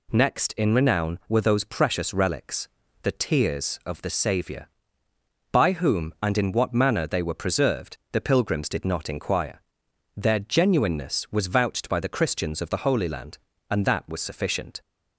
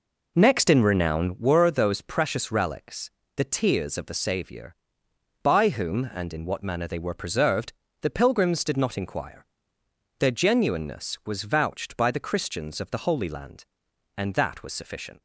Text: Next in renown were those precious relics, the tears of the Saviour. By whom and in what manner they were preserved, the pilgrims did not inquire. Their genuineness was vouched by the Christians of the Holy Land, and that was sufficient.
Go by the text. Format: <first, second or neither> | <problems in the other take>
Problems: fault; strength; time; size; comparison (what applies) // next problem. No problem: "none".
first | starts louder than the rest; noticeable; until 1.4 s; 4.5 dB